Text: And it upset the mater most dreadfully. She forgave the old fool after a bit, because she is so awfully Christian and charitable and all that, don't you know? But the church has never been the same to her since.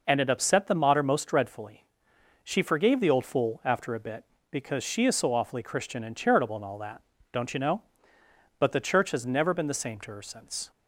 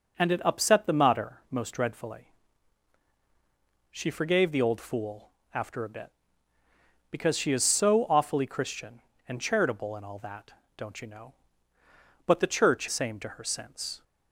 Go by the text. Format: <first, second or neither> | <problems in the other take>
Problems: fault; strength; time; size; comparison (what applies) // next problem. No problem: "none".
first | pauses between "fool" and "after"; slight; at 5.3 s; 0.22 s long // skips "has never been the"; at 12.8 s